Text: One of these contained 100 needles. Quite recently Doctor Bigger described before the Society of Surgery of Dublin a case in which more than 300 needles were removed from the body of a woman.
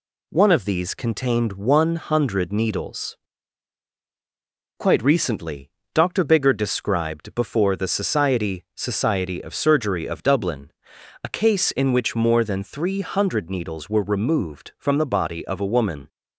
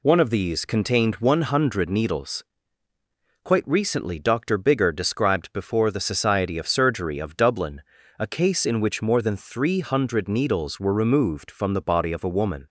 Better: second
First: pauses between "recently" and "Doctor"; slight; at 5.6 s; 0.24 s long // says "Society" twice; at 8.7 s // pauses between "Dublin" and "a"; noticeable; at 10.7 s; 0.50 s long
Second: pauses between "Dublin" and "a"; slight; at 7.8 s; 0.36 s long

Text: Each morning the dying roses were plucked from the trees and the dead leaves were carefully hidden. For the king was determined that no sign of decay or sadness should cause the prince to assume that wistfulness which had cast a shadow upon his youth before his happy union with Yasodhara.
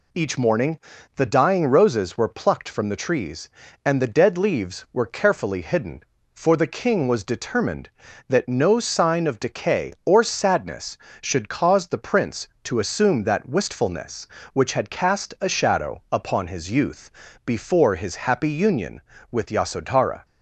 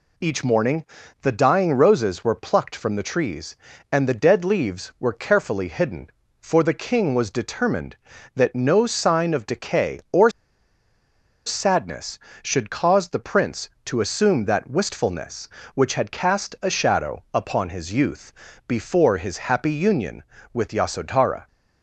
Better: first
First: pauses between "morning" and "the"; slight; at 0.8 s; 0.34 s long // pauses between "youth" and "before"; slight; at 17.1 s; 0.34 s long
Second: pauses between "morning" and "the"; slight; at 0.8 s; 0.34 s long // pauses between "or" and "sadness"; at 10.3 s; 1.1 s long // pauses between "youth" and "before"; slight; at 18.3 s; 0.34 s long

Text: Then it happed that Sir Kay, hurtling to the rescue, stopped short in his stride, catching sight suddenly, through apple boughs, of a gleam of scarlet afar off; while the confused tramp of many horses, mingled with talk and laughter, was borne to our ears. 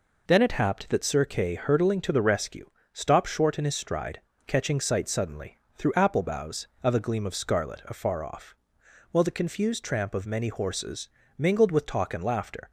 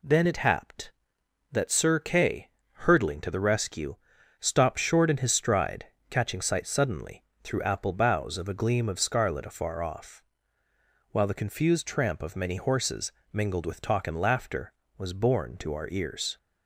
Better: second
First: stops before "was borne to our ears"; at 12.6 s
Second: none

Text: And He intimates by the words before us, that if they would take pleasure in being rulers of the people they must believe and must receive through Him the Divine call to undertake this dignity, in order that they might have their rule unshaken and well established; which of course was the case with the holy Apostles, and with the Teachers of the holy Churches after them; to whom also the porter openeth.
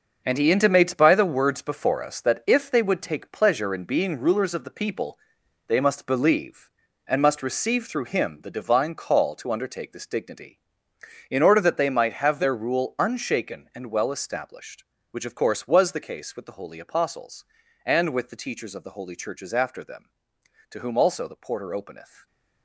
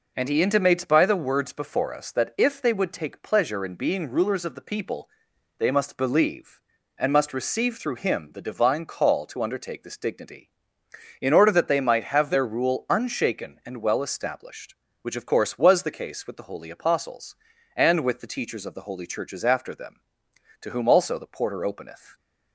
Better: second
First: gets quieter; strong; throughout; 9.5 dB // pauses between "people" and "they"; noticeable; at 5.1 s; 0.50 s long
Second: pauses between "people" and "they"; noticeable; at 5.0 s; 0.50 s long

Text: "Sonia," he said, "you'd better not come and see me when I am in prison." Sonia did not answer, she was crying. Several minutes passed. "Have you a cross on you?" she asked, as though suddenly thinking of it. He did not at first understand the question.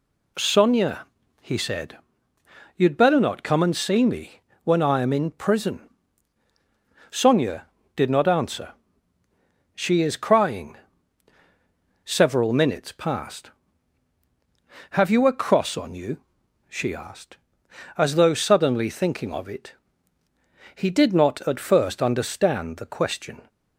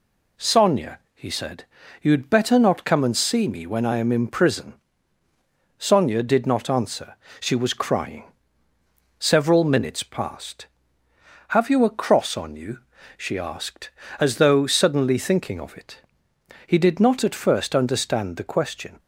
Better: second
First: pauses between "me" and "when"; slight; at 4.3 s; 0.24 s long // says "is" for "was"; at 10.0 s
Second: none

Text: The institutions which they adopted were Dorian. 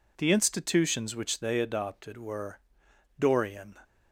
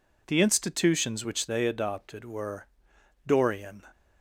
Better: neither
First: pauses between "were" and "Dorian"; noticeable; at 2.6 s; 0.58 s long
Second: pauses between "were" and "Dorian"; noticeable; at 2.6 s; 0.58 s long

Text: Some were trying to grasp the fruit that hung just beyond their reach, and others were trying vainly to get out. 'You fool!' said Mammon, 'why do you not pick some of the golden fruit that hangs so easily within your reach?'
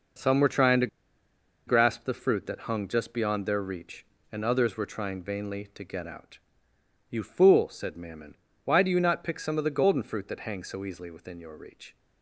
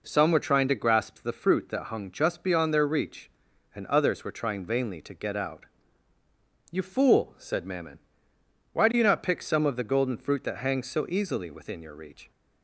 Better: second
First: pauses between "to" and "grasp"; noticeable; at 0.8 s; 0.79 s long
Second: none

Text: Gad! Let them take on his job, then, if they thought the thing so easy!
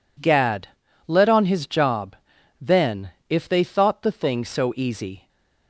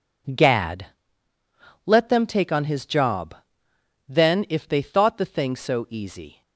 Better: second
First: skips "them take"; at 1.2 s // stays silent after the last word; slight; from 5.1 s on; 0.5 s long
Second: none

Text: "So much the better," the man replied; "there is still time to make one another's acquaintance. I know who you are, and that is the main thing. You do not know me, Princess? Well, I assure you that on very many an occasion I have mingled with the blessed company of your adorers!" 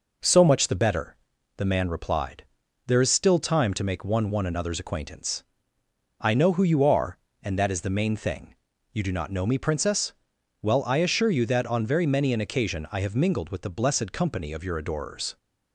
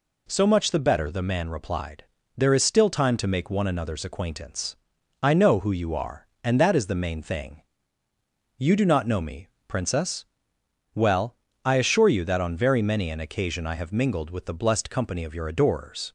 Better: second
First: says "one" twice; at 4.2 s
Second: none

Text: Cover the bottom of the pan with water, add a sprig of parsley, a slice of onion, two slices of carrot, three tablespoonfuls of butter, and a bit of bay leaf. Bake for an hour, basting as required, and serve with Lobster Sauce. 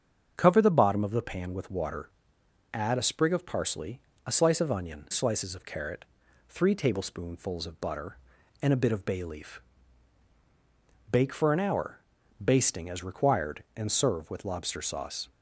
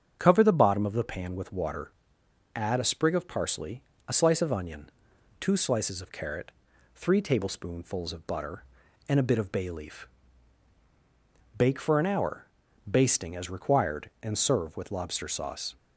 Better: second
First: starts louder than the rest; strong; until 1.3 s; 7.5 dB // skips "two"; at 5.0 s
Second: starts louder than the rest; strong; until 1.2 s; 7.5 dB

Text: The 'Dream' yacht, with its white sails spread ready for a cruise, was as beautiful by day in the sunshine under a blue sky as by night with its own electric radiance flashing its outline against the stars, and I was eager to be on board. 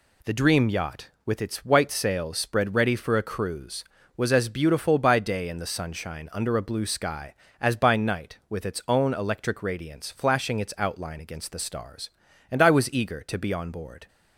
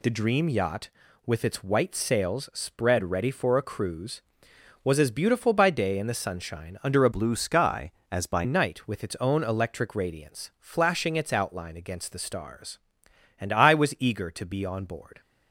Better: first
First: none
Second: changes voice from "blue" to "by"; from 7.1 to 8.4 s; 1.3 s long

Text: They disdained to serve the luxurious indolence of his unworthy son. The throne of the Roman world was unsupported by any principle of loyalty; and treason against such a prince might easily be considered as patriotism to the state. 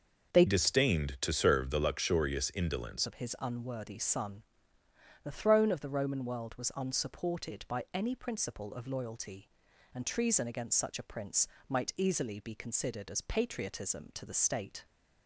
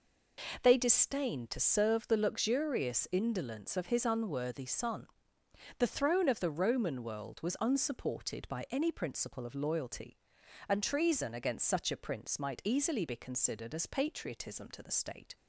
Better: second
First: starts louder than the rest; until 1.4 s; 6 dB // changes voice from "disdained" to "indolence"; from 0.4 to 3.0 s; 2.6 s long // pauses between "prince" and "might"; slight; at 11.4 s; 0.22 s long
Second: none

